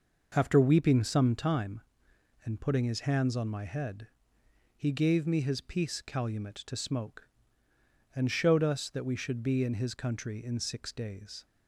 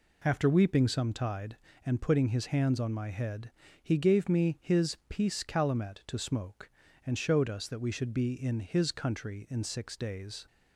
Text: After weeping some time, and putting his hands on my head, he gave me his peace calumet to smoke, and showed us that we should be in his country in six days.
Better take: first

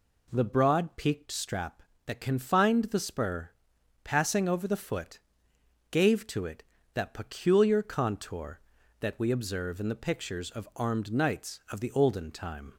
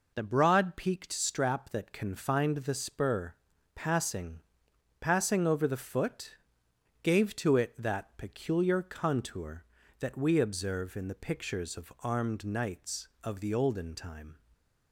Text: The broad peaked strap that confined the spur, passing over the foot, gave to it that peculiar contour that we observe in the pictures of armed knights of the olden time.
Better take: first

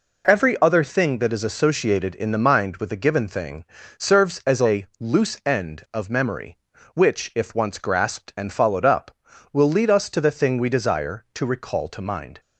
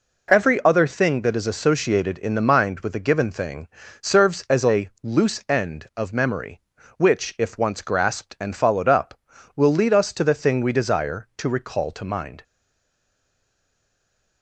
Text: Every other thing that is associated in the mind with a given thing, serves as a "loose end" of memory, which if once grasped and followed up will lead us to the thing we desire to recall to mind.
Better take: first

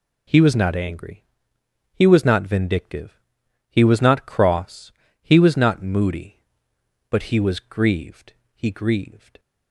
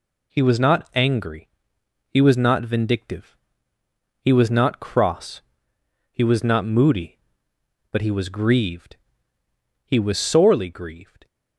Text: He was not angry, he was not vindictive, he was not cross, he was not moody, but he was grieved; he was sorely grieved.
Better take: second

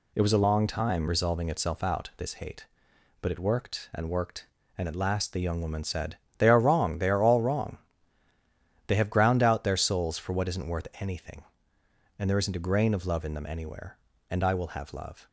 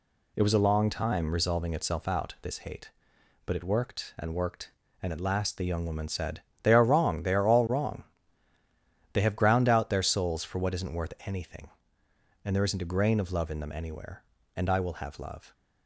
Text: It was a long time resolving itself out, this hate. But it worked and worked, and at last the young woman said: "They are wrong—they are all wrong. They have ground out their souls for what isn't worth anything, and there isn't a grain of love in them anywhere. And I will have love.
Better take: neither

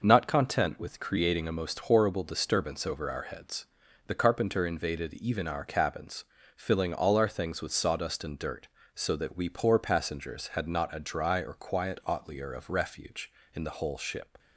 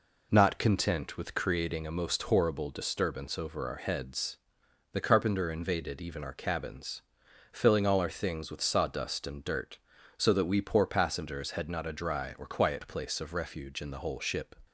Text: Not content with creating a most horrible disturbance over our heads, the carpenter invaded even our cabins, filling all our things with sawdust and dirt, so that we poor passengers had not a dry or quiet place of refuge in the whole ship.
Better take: second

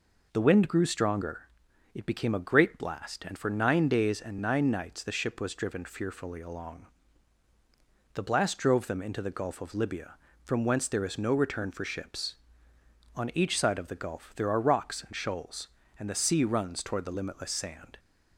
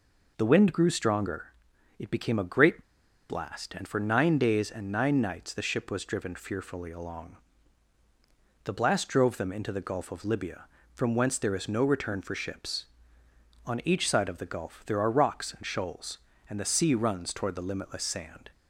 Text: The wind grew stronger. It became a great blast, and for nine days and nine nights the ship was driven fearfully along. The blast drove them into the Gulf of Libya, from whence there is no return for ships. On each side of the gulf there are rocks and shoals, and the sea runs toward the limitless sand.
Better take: first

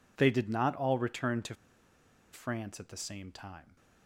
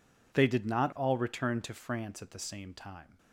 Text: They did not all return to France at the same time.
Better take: second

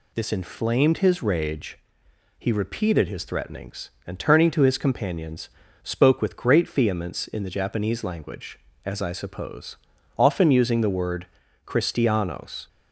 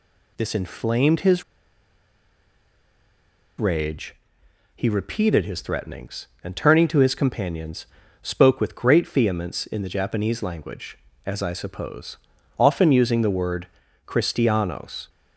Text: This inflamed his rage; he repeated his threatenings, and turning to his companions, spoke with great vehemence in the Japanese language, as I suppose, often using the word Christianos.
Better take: first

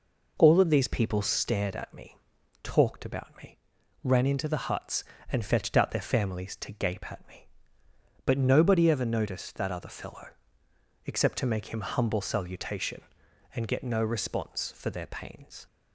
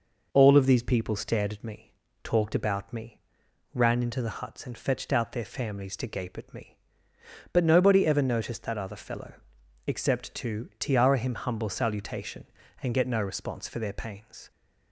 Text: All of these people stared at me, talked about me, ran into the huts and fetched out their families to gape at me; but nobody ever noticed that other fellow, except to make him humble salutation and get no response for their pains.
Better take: first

